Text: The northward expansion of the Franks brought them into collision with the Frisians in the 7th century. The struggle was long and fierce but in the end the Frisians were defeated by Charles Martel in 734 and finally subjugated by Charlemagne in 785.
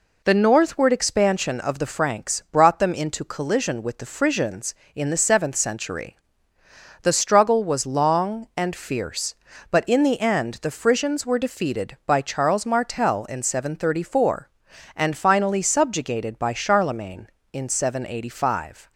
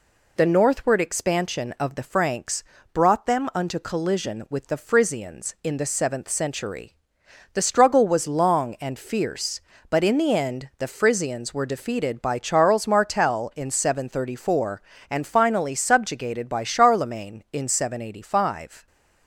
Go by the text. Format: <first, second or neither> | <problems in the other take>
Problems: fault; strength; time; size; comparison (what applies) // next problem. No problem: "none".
first | pauses between "Franks" and "brought"; slight; at 2.6 s; 0.32 s long // says "unto" for "into"; at 3.5 s